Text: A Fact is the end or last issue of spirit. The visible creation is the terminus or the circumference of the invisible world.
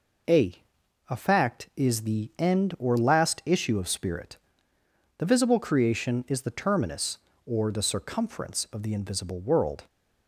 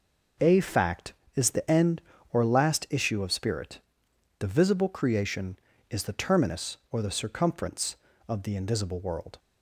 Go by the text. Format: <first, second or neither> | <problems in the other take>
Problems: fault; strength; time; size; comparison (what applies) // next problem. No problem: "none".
second | says "A" twice; at 1.1 s